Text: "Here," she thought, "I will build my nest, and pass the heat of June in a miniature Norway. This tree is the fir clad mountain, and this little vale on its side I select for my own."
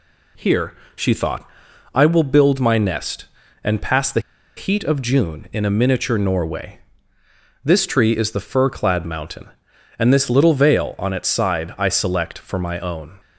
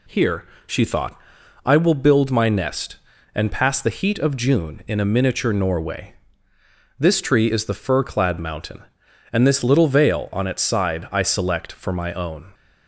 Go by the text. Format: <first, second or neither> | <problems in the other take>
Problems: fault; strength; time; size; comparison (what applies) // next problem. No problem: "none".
second | pauses between "the" and "heat"; at 4.2 s; 0.36 s long